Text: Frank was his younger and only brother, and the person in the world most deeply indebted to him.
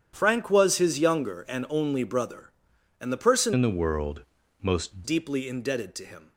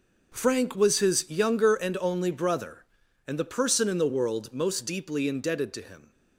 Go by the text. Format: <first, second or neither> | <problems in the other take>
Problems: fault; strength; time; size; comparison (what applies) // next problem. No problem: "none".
second | starts louder than the rest; strong; until 1.1 s; 9.5 dB // changes voice from "in" to "most"; from 3.5 to 5.0 s; 1.5 s long // pauses between "world" and "most"; at 4.2 s; 0.38 s long